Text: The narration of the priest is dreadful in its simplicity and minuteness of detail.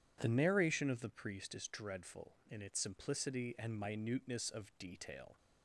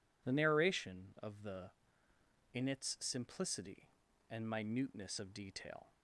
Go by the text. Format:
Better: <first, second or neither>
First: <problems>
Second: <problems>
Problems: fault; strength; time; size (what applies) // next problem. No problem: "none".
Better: first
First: none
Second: skips "priest is dreadful"; at 2.1 s